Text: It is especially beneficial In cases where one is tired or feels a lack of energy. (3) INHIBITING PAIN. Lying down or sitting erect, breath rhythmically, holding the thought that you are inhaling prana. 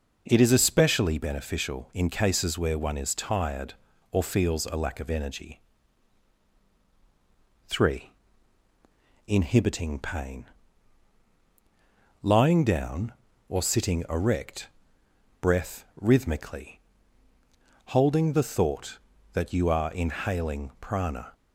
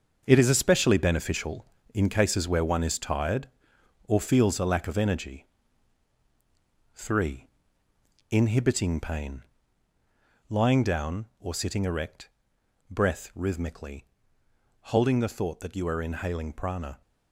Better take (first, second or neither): first